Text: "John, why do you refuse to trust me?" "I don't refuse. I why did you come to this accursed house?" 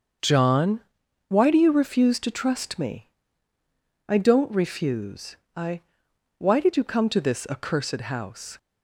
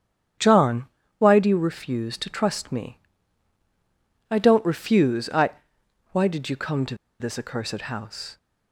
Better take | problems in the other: first | starts louder than the rest; strong; until 1.7 s; 8.5 dB; also in the first // pauses between "I" and "why"; noticeable; at 5.5 s; 0.62 s long; noticeable in the first // pauses between "to" and "this"; slight; at 6.9 s; 0.25 s long

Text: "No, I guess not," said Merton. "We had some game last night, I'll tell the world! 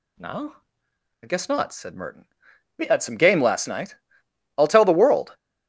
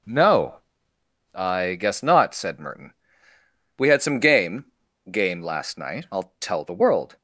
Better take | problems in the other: first | says "game" twice; at 5.1 s

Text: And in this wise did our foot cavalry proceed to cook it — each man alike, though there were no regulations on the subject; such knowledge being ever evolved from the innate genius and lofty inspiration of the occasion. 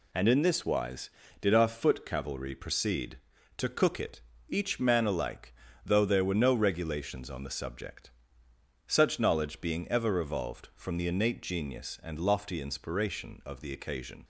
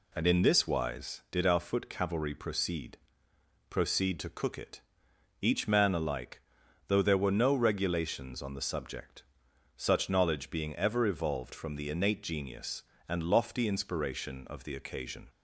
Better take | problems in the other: first | says "proceed" twice; at 3.6 s

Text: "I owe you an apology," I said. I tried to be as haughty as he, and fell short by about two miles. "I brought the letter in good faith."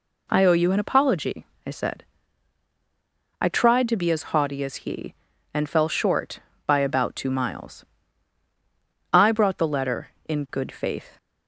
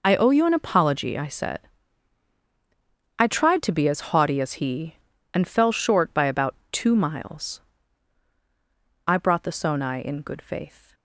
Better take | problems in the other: first | pauses between "about" and "two"; slight; at 6.5 s; 0.16 s long // says "sonai" for "letter"; at 9.5 s

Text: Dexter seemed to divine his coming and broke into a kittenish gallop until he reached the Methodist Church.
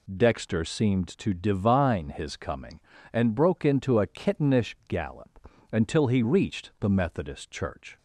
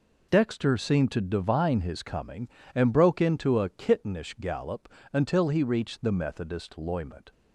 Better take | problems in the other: first | pauses between "gallop" and "until"; slight; at 4.8 s; 0.24 s long; slight in the first // says "Loyment" for "Church"; at 6.7 s

